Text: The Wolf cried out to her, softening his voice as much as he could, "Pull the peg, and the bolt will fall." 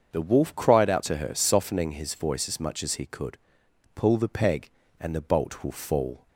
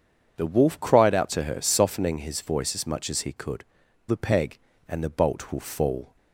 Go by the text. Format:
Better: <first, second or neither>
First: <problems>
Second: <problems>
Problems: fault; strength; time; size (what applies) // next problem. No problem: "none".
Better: first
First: starts louder than the rest; until 1.1 s; 7 dB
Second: starts louder than the rest; strong; until 1.4 s; 7.5 dB // skips "Pull"; at 3.8 s